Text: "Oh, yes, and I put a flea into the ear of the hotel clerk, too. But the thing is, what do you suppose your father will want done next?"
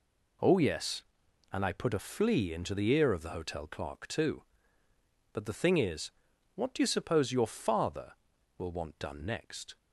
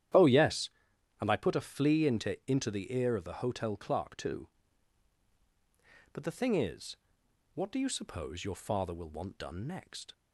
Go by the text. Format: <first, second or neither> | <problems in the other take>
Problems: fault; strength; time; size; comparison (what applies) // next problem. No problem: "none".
first | starts louder than the rest; strong; until 1.6 s; 11 dB // says "into" twice; at 2.4 s